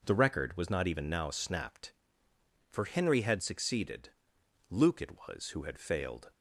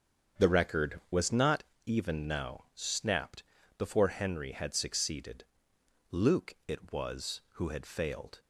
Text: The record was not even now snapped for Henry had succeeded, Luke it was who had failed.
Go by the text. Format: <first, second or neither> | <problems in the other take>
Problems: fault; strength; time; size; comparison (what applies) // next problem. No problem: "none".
first | starts louder than the rest; strong; until 1.4 s; 7 dB // pauses between "not" and "even"; slight; at 1.6 s; 0.22 s long // says "before" for "for"; at 3.7 s